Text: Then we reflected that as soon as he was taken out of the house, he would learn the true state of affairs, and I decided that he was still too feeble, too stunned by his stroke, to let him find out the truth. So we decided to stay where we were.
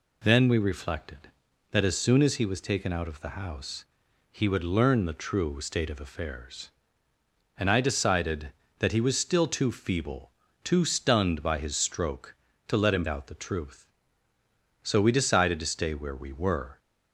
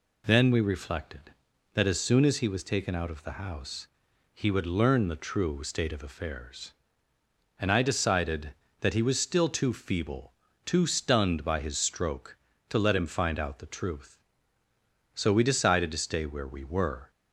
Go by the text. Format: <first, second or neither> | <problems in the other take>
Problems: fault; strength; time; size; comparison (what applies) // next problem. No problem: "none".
second | skips "find"; at 13.0 s